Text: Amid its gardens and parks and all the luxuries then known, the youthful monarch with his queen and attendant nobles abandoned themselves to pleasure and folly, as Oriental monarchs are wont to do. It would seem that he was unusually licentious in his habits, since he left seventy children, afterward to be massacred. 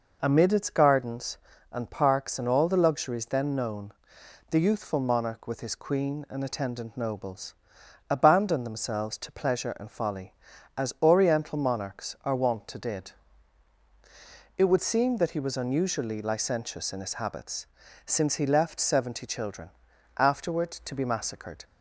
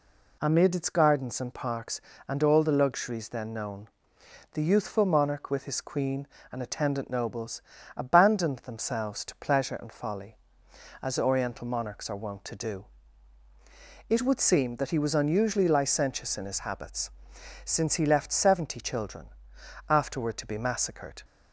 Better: second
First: pauses between "nobles" and "abandoned"; noticeable; at 7.5 s; 0.56 s long // says "did" for "do"; at 12.7 s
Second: pauses between "nobles" and "abandoned"; slight; at 7.6 s; 0.36 s long

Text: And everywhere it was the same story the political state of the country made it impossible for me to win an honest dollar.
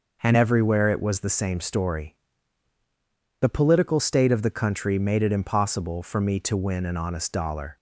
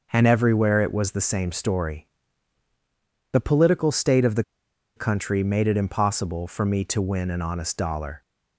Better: first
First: pauses between "story" and "the"; at 2.1 s; 1.2 s long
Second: pauses between "story" and "the"; at 2.0 s; 1.2 s long // pauses between "the" and "country"; noticeable; at 4.4 s; 0.54 s long

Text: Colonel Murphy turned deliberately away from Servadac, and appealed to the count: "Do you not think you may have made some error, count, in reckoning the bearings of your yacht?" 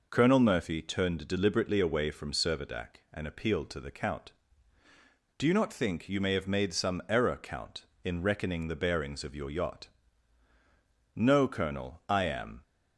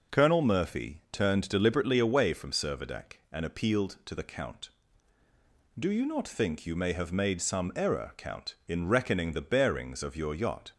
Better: second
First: goes on to say "No colonel I am"; from 11.1 s on; 1.4 s long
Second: none

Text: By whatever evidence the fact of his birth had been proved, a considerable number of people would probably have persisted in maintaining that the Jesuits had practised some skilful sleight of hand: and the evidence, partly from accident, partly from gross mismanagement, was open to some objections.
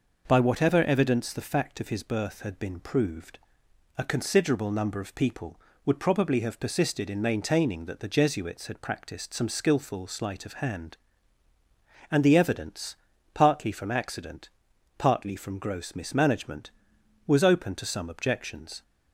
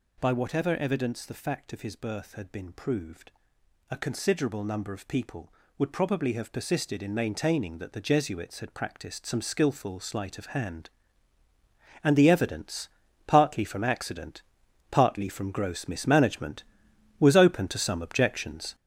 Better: first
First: none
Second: gets louder; strong; throughout; 7.5 dB

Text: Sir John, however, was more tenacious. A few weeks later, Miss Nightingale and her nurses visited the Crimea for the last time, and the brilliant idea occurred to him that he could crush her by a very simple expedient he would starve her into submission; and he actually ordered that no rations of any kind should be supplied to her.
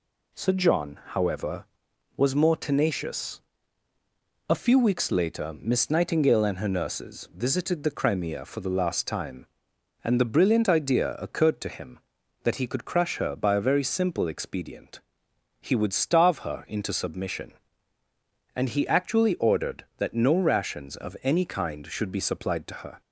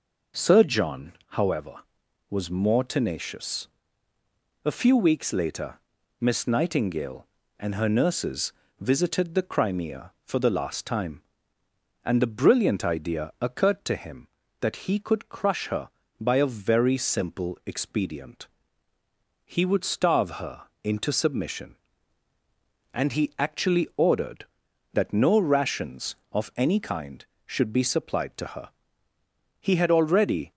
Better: first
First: pauses between "expedient" and "he"; noticeable; at 15.0 s; 0.64 s long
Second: pauses between "nurses" and "visited"; slight; at 8.5 s; 0.30 s long // pauses between "expedient" and "he"; noticeable; at 18.4 s; 0.98 s long // pauses between "her" and "into"; slight; at 20.6 s; 0.20 s long // goes on to say "He had already"; noticeable; from 29.6 s on; 0.90 s long

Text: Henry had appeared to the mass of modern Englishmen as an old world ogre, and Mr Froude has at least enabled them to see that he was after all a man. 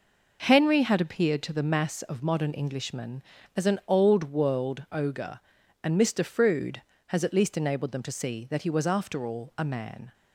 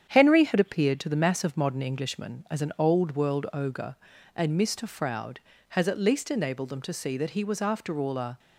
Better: first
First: none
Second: starts louder than the rest; strong; until 1.1 s; 8.5 dB // stops before "man"; at 8.3 s

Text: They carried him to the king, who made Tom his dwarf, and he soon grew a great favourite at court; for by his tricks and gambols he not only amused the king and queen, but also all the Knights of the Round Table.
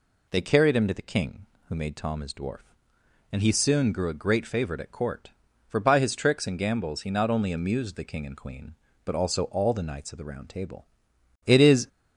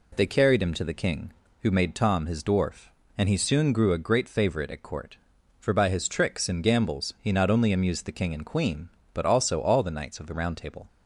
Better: second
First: goes on to say "It is"; slight; from 11.4 s on; 0.42 s long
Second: none

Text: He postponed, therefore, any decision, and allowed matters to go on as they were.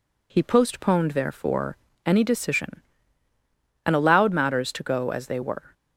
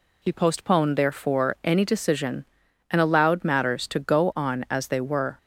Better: second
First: skips "on"; at 5.1 s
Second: none

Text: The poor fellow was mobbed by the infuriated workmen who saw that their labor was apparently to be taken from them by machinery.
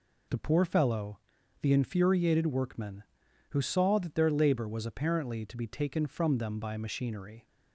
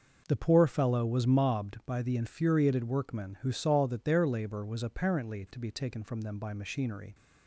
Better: second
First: skips "was mobbed by"; at 1.4 s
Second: none

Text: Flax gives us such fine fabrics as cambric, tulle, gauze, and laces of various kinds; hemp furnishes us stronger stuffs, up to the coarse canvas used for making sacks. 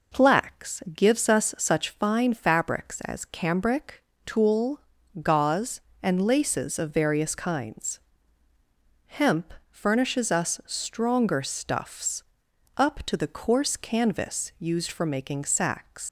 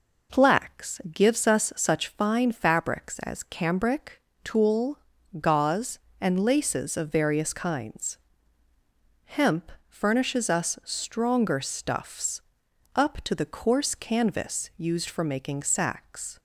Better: second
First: pauses between "hemp" and "furnishes"; slight; at 9.5 s; 0.16 s long // leaves "sacks" unfinished; at 16.0 s; 115 ms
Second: pauses between "hemp" and "furnishes"; slight; at 9.7 s; 0.16 s long

